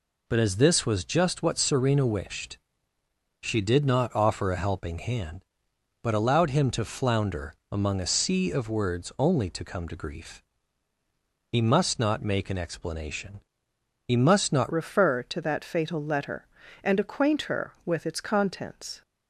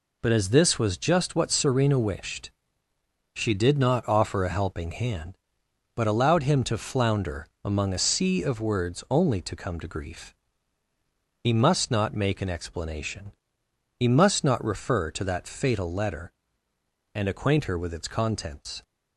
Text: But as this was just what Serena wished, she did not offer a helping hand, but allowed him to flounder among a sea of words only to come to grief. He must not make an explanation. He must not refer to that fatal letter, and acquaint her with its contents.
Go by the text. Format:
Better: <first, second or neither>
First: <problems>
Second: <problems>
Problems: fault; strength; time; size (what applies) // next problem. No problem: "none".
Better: second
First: pauses between "flounder" and "among"; slight; at 7.5 s; 0.16 s long // changes voice at "refer"; from 14.7 s on; 4.3 s long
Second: pauses between "flounder" and "among"; slight; at 7.4 s; 0.16 s long